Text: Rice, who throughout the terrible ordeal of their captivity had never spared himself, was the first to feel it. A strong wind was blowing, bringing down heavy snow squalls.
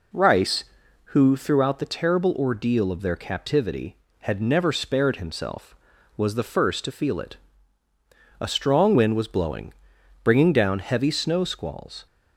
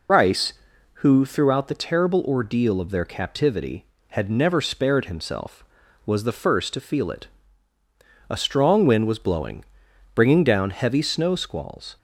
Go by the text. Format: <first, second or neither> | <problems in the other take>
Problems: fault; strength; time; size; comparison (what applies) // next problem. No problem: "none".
first | loses the start of "Rice"; at 0.0 s; 75 ms